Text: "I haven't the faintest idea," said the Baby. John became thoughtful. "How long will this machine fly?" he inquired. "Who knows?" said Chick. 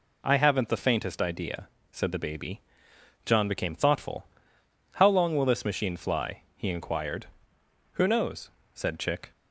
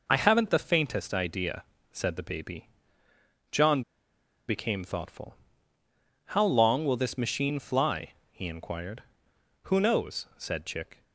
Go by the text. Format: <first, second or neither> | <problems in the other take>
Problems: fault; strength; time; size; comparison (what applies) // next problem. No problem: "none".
first | pauses between "John" and "became"; noticeable; at 3.8 s; 0.65 s long